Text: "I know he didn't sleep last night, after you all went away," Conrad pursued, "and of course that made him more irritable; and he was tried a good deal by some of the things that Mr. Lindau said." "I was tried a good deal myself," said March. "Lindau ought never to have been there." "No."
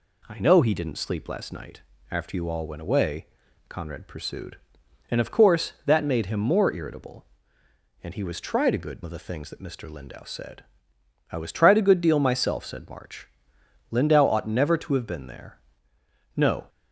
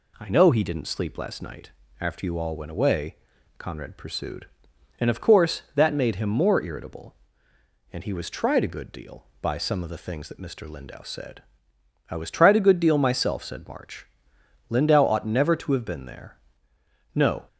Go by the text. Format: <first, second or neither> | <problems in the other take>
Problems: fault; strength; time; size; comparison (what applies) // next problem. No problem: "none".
second | skips "deal by some"; at 9.0 s